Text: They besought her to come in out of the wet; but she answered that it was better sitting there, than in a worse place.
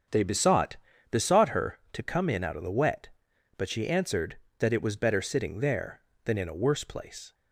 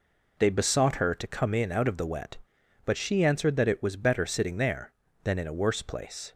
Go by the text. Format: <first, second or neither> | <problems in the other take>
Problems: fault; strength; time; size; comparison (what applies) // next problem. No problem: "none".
second | starts louder than the rest; strong; until 1.4 s; 7.5 dB // says "besought" twice; at 1.0 s